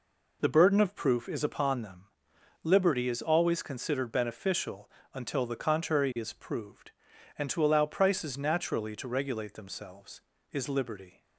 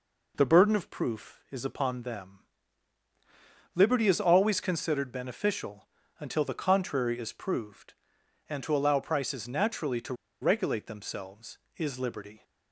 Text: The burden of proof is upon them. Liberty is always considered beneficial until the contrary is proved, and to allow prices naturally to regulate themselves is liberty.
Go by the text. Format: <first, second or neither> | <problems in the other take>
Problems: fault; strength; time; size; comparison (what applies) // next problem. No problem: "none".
first | pauses between "beneficial" and "until"; slight; at 5.8 s; 0.34 s long; slight in the first // pauses between "to" and "regulate"; slight; at 10.1 s; 0.27 s long